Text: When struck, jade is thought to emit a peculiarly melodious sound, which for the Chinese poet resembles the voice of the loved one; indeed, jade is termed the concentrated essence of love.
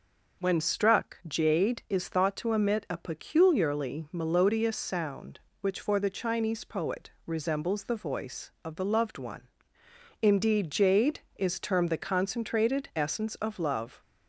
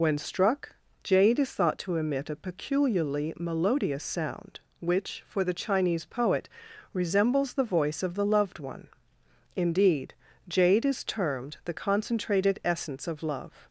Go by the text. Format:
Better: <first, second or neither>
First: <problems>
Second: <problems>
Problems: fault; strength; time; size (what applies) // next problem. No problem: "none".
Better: first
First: pauses between "poet" and "resembles"; slight; at 7.1 s; 0.16 s long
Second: loses the start of "When"; at 0.0 s; 75 ms // pauses between "poet" and "resembles"; noticeable; at 6.4 s; 0.46 s long